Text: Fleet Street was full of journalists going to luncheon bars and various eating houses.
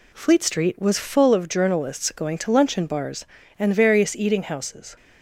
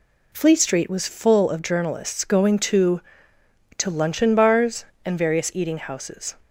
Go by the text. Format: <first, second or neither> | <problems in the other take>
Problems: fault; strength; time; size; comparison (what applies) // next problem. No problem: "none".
first | says "to" twice; at 3.7 s